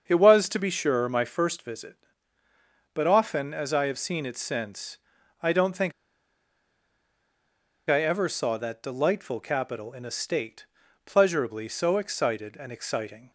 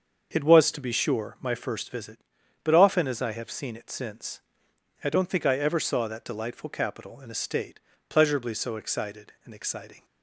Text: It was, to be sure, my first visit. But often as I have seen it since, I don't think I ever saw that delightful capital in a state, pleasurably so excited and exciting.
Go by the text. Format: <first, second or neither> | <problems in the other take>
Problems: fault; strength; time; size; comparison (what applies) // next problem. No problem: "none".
second | starts louder than the rest; until 1.1 s; 6.5 dB; also in the second // pauses between "think" and "I"; strong; at 5.9 s; 1.9 s long